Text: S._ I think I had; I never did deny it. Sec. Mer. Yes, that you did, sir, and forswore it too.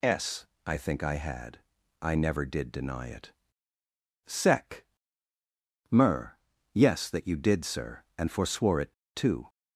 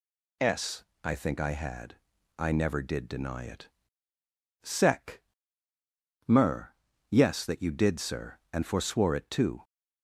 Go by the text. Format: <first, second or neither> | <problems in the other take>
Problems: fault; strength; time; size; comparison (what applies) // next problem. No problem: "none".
second | pauses between "it" and "too"; slight; at 8.9 s; 0.20 s long